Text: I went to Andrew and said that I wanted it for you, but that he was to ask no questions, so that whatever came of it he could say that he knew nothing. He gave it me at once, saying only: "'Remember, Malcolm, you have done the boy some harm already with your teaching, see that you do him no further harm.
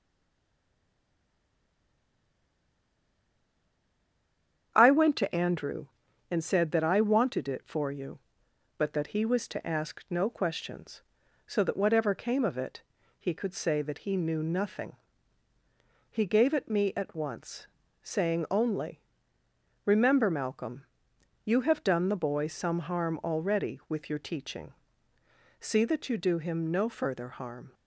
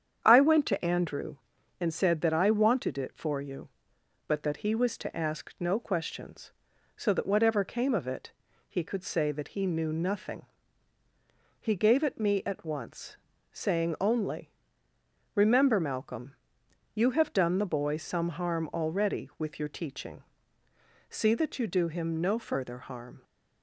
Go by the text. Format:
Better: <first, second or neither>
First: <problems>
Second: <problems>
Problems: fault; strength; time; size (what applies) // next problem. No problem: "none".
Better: second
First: stays silent before the first word; strong; until 4.7 s; 4.7 s long // starts louder than the rest; strong; until 5.7 s; 8.5 dB // pauses between "it" and "he"; at 12.8 s; 0.38 s long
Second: starts louder than the rest; strong; until 1.2 s; 8.5 dB // pauses between "it" and "he"; at 8.3 s; 0.38 s long